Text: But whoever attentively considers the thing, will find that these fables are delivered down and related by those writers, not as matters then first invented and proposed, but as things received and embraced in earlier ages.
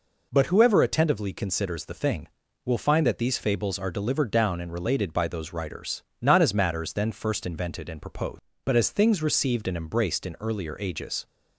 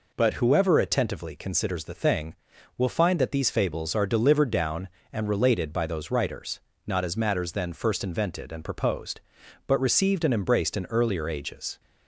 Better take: first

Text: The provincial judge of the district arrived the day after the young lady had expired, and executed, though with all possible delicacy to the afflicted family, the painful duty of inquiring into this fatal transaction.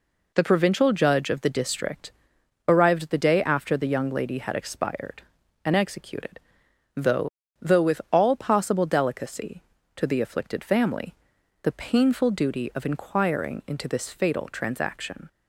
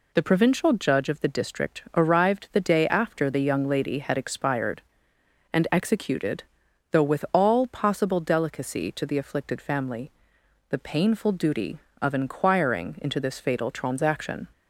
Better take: second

